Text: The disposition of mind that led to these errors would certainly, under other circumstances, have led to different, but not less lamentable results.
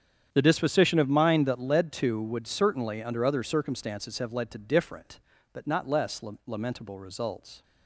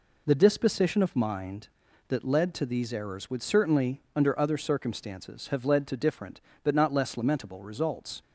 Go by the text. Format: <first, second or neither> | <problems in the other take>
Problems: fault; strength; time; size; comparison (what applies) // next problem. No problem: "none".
second | starts louder than the rest; strong; until 1.3 s; 8.5 dB // skips "these errors"; at 2.2 s // pauses between "less" and "lamentable"; slight; at 6.2 s; 0.24 s long